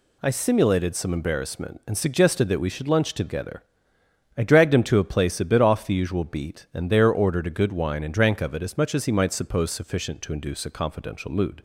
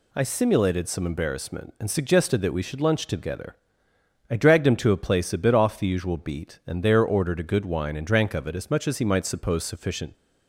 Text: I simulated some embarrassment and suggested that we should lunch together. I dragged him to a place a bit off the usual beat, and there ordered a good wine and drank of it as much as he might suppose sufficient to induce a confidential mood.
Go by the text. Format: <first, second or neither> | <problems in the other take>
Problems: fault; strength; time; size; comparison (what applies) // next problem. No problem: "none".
first | stops before "to induce a confidential mood"; at 10.1 s